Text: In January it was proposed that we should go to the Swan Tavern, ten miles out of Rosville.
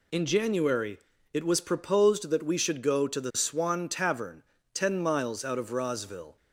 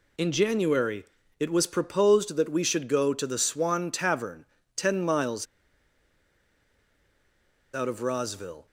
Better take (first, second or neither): first